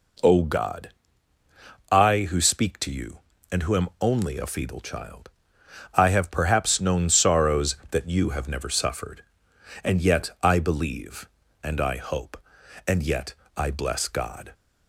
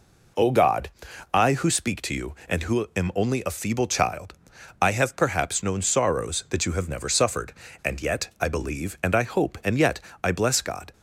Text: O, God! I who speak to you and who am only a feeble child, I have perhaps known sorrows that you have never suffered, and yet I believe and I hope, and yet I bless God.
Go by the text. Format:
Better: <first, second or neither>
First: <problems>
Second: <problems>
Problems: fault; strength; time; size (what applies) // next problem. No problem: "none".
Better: neither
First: pauses between "yet" and "I"; slight; at 13.3 s; 0.22 s long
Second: pauses between "yet" and "I"; slight; at 9.9 s; 0.24 s long